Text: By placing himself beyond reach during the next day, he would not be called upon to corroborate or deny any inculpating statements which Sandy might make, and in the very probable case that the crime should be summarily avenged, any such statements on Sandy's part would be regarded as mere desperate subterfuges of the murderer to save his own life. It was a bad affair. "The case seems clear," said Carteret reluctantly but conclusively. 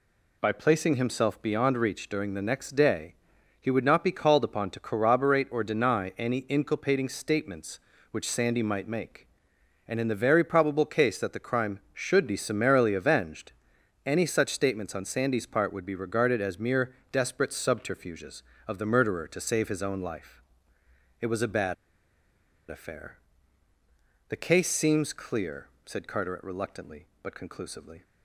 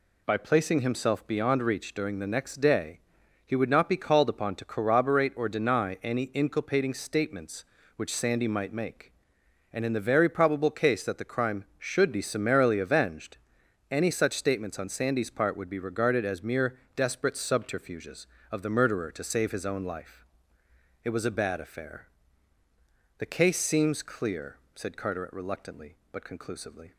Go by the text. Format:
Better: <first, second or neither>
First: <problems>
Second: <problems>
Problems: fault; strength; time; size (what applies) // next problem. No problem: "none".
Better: second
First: pauses between "mere" and "desperate"; slight; at 16.9 s; 0.18 s long // pauses between "bad" and "affair"; noticeable; at 21.7 s; 0.94 s long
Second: pauses between "mere" and "desperate"; slight; at 16.7 s; 0.18 s long